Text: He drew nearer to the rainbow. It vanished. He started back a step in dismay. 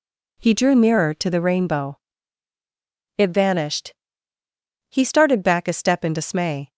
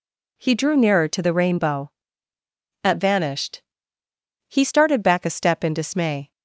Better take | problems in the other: first | says "At" for "It"; at 2.8 s

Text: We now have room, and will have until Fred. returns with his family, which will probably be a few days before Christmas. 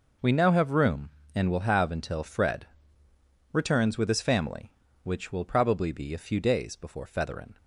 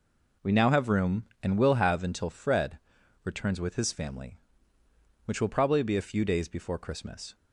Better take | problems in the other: second | says "Featherin" for "Christmas"; at 7.0 s

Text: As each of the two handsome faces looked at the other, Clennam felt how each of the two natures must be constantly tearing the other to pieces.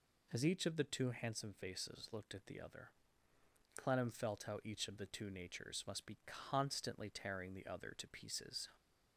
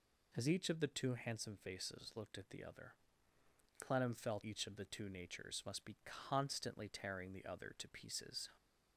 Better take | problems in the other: first | skips "how"; at 4.4 s

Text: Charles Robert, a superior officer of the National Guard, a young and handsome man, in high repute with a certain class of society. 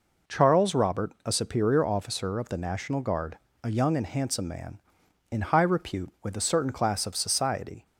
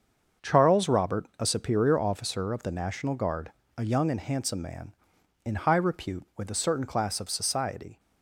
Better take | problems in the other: first | gets quieter; strong; throughout; 9 dB

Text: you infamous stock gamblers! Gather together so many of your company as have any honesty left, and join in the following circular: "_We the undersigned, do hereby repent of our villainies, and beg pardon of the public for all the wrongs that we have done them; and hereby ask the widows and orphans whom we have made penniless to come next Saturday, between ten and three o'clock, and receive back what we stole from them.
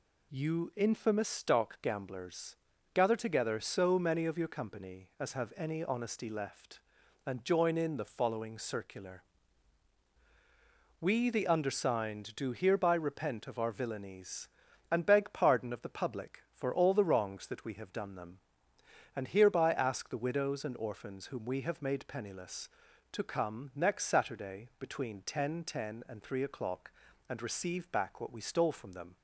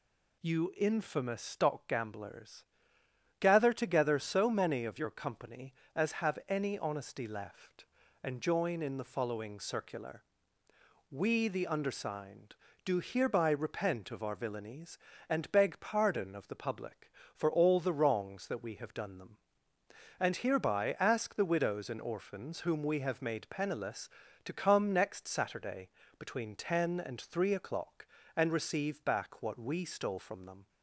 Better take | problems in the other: second | says "ten" twice; at 25.6 s

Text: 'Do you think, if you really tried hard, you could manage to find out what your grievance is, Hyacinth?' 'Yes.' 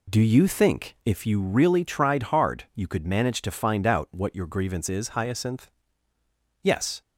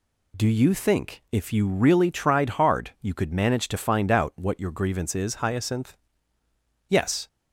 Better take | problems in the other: second | starts louder than the rest; slight; until 1.3 s; 2 dB

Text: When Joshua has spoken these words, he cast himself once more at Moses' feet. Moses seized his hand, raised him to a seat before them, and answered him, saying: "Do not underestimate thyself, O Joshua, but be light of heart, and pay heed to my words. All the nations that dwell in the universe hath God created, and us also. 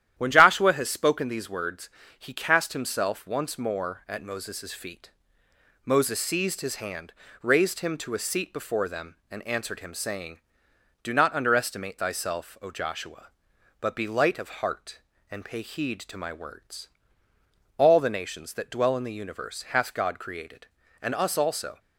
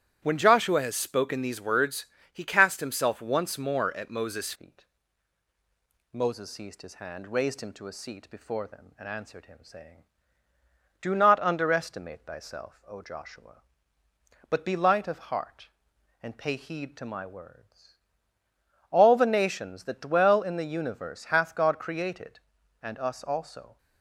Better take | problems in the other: first | starts louder than the rest; strong; until 1.2 s; 12 dB; strong in the first // changes voice at "feet"; from 4.5 s on; 19.2 s long

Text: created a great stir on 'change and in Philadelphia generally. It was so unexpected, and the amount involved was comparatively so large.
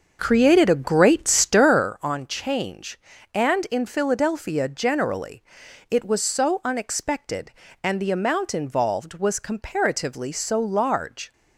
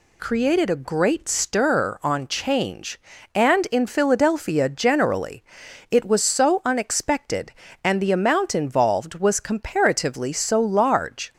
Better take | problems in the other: second | starts louder than the rest; until 1.9 s; 6.5 dB

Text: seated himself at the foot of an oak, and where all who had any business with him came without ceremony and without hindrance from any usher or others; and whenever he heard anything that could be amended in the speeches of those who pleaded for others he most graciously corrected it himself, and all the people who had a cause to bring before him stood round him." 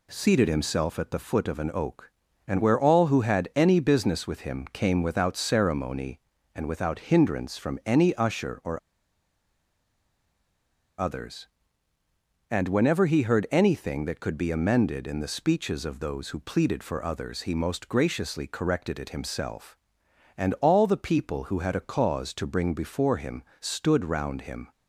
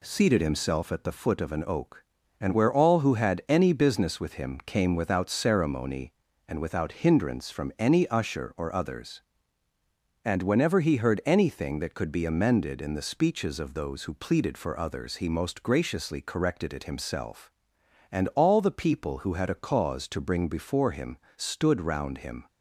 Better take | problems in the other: second | pauses between "or" and "others"; strong; at 8.7 s; 2.2 s long // pauses between "him" and "stood"; slight; at 23.4 s; 0.16 s long; slight in the second

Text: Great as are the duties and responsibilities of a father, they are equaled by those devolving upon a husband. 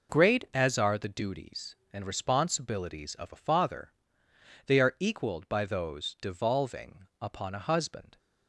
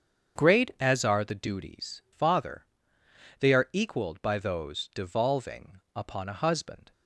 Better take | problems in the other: first | starts louder than the rest; strong; until 1.4 s; 7.5 dB // skips "and responsibilities of a"; at 2.0 s // pauses between "devolving" and "upon"; slight; at 5.7 s; 0.16 s long; slight in the first

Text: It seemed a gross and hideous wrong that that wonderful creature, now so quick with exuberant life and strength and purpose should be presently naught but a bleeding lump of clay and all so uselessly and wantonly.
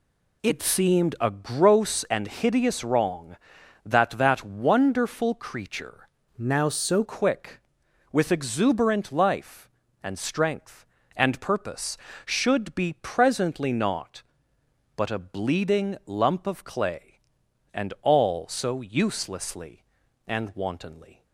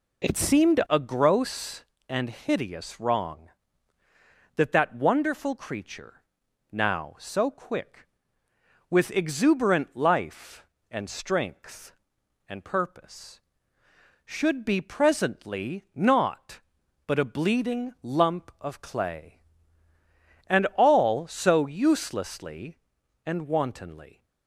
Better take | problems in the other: second | changes voice from "now" to "so"; from 6.3 to 7.0 s; 0.7 s long

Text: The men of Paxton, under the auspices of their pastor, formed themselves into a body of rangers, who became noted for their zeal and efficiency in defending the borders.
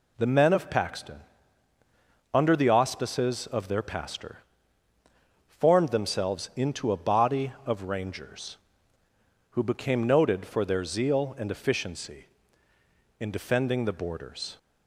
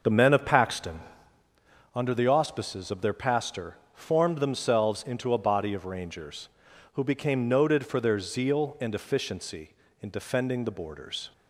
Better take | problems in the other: first | starts louder than the rest; noticeable; until 1.6 s; 6 dB

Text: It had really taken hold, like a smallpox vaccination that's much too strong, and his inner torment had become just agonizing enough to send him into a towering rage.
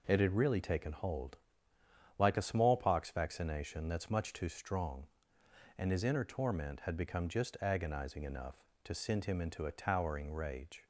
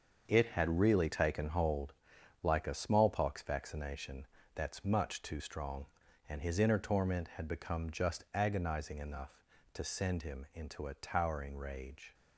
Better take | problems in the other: first | gets quieter; strong; throughout; 8.5 dB // pauses between "vaccination" and "that's"; slight; at 4.2 s; 0.30 s long

